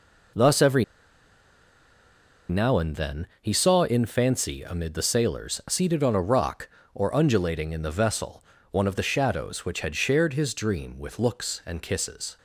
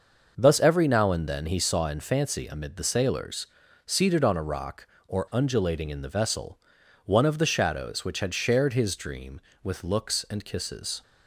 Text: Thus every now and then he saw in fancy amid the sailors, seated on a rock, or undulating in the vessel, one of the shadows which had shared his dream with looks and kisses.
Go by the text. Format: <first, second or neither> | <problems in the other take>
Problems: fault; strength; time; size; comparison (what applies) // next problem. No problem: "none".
second | pauses between "every" and "now"; strong; at 0.8 s; 1.6 s long